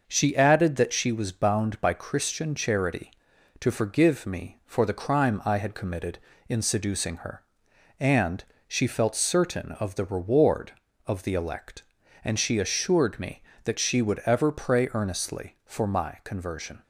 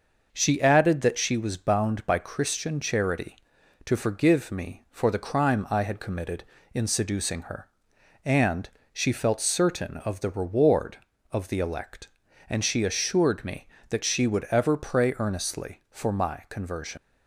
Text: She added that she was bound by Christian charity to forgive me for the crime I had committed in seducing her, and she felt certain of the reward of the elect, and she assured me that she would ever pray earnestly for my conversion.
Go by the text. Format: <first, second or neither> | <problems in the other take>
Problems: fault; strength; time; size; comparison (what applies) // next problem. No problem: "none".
first | pauses between "and" and "she"; slight; at 8.6 s; 0.24 s long; slight in the first // leaves "conversion" unfinished; at 16.9 s; 105 ms